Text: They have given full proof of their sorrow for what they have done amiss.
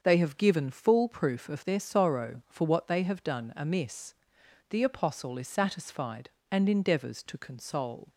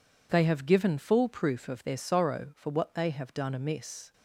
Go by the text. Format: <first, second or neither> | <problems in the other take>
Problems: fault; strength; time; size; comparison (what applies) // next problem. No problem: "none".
second | starts louder than the rest; until 1.0 s; 7 dB // goes on to say "The Apostle is satisfied and endeavours to console"; strong; from 4.6 s on; 3.4 s long